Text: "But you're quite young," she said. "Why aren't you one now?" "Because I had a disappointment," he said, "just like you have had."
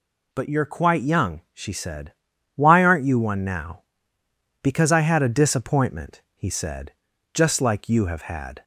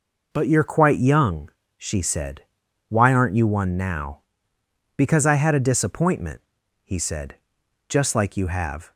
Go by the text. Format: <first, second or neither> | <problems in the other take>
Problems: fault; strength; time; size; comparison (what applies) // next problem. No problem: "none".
first | stops before "had"; at 8.9 s